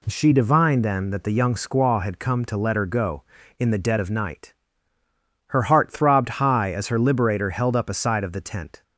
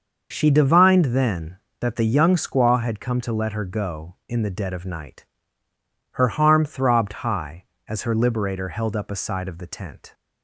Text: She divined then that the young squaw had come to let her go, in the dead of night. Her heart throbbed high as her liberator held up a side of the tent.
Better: first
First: none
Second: starts louder than the rest; until 1.3 s; 6 dB // says "harm" for "heart"; at 6.2 s

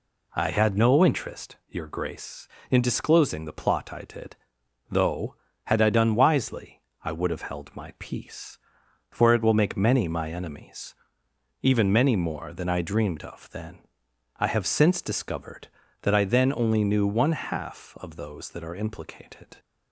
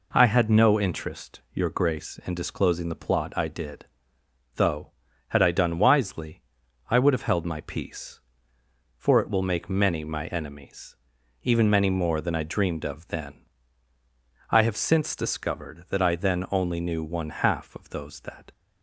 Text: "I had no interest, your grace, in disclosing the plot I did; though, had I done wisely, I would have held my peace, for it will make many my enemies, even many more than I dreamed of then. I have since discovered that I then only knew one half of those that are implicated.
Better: first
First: none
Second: stops before "are implicated"; at 18.5 s

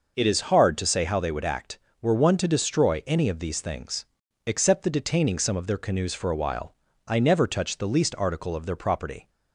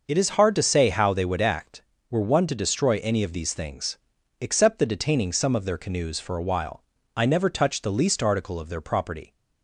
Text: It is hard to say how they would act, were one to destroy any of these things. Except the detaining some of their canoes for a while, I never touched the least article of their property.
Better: neither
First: none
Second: none

